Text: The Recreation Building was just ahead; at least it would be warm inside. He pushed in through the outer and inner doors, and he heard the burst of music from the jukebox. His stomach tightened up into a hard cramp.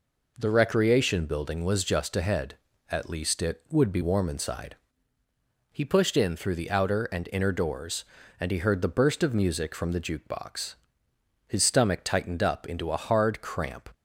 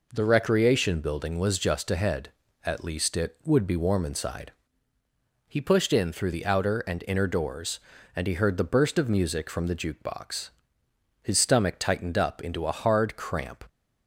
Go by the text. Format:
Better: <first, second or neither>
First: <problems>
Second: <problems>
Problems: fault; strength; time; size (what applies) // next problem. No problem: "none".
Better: neither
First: none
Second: none